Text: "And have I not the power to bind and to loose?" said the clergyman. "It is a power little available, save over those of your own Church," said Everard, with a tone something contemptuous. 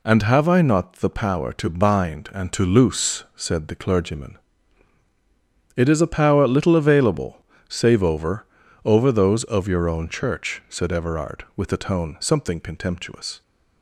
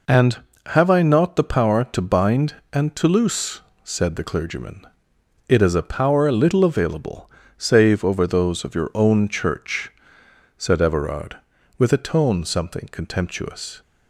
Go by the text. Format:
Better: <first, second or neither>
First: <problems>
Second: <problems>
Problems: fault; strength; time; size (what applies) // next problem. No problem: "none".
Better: second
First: says "over" twice; at 8.8 s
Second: none